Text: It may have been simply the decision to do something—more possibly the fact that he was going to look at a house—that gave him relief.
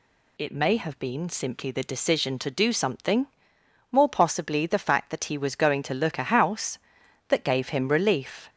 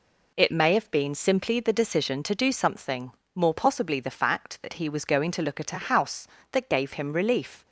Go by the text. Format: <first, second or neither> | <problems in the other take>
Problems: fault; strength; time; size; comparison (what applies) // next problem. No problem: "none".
second | skips "at"; at 6.1 s